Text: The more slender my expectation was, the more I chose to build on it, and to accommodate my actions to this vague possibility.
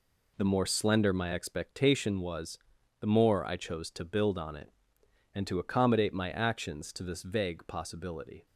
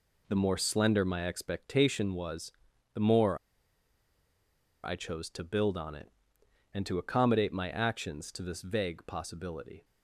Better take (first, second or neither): first